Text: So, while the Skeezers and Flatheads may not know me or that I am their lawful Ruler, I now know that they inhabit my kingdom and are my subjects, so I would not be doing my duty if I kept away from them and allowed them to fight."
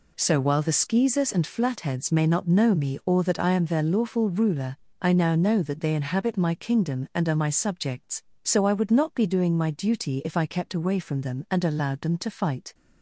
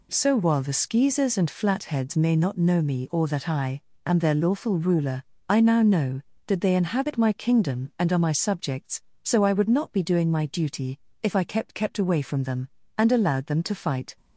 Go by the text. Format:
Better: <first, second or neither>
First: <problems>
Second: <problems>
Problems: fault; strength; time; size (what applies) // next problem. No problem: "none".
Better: first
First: none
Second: pauses between "I" and "am"; slight; at 3.7 s; 0.24 s long // pauses between "duty" and "if"; slight; at 10.9 s; 0.24 s long // says "kept" twice; at 11.7 s